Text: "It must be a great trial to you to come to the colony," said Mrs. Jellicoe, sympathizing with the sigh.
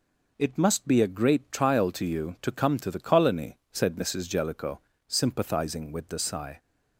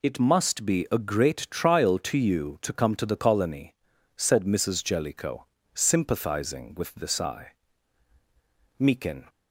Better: first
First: none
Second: goes on to say "Meekin"; from 8.7 s on; 0.52 s long

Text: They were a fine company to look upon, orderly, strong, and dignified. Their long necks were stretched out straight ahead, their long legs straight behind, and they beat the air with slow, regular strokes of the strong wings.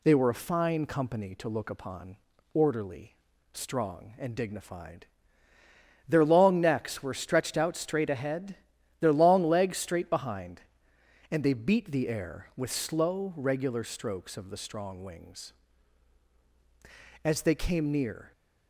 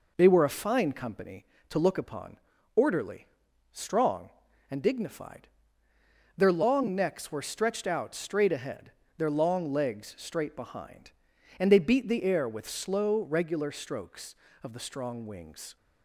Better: second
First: goes on to say "As they came near"; noticeable; from 17.2 s on; 1.0 s long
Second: none

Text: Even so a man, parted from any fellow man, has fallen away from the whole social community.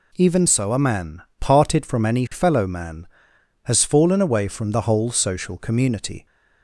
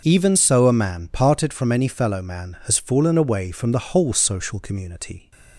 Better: neither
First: none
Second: none

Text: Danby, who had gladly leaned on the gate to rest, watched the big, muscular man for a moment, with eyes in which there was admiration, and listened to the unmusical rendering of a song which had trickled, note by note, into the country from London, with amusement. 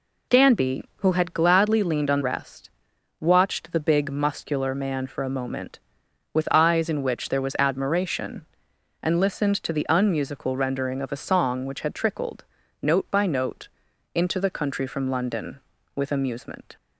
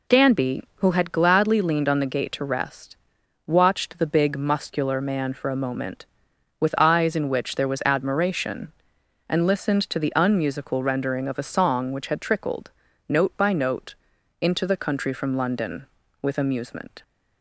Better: second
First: skips "the gate to"; at 2.2 s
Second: none

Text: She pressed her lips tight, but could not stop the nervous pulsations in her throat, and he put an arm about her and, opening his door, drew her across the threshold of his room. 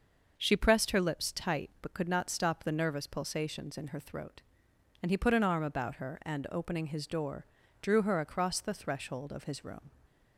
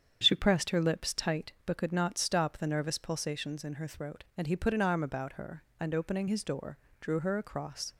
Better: first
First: starts louder than the rest; noticeable; until 1.3 s; 6 dB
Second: starts louder than the rest; strong; until 1.2 s; 8 dB // stops before "the threshold of his room"; at 7.9 s

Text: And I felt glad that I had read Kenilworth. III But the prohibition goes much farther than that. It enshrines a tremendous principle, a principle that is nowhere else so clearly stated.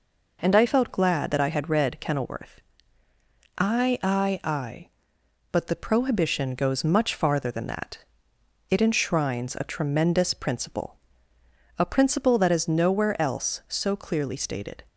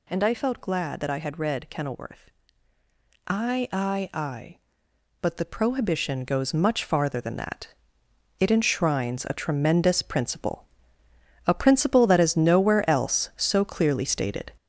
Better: first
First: none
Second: gets louder; noticeable; throughout; 6 dB

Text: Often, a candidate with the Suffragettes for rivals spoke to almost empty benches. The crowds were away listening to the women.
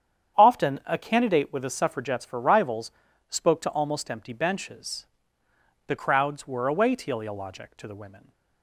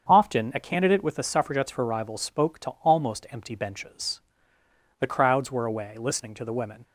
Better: second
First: starts louder than the rest; strong; until 1.4 s; 8.5 dB // pauses between "rivals" and "spoke"; at 2.9 s; 0.38 s long // says "teleologic" for "listening"; at 6.9 s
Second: starts louder than the rest; until 1.1 s; 7 dB

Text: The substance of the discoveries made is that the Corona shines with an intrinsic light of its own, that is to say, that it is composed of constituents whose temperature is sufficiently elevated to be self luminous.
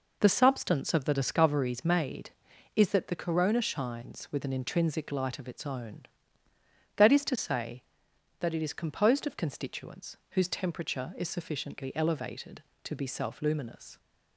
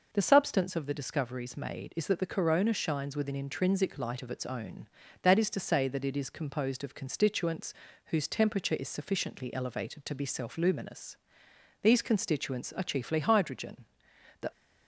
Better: first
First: none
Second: pauses between "constituents" and "whose"; slight; at 7.7 s; 0.32 s long // goes on to say "These constituents are chiefly hydrogen the"; strong; from 11.8 s on; 2.6 s long

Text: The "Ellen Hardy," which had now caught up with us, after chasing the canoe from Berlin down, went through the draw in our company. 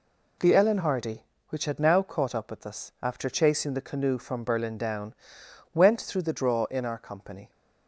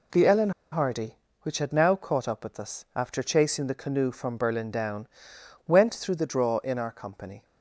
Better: first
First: none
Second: pauses between "Ellen" and "Hardy"; slight; at 0.4 s; 0.21 s long

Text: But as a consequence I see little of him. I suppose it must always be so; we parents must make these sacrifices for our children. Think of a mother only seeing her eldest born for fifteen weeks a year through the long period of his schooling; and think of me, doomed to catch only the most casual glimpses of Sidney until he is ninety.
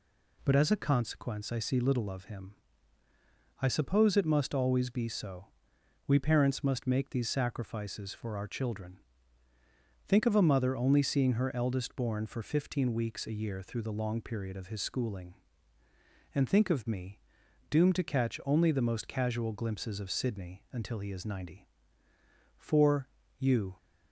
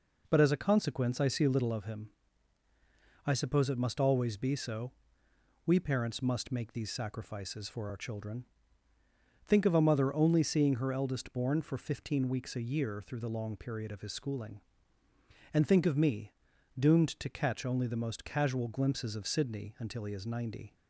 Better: second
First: goes on to say "For you"; noticeable; from 22.5 s on; 1.1 s long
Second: none

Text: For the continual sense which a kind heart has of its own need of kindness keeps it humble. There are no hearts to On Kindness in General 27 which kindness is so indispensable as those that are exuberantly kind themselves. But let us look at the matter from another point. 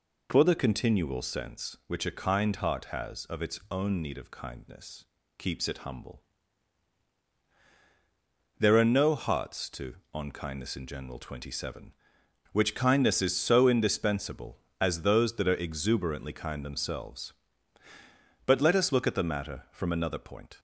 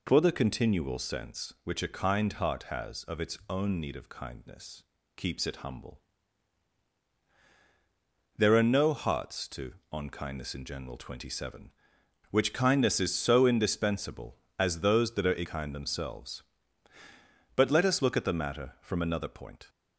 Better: first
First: pauses between "kindness" and "keeps"; slight; at 5.0 s; 0.34 s long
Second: pauses between "kindness" and "keeps"; slight; at 4.8 s; 0.34 s long // skips "exuberantly"; at 15.4 s

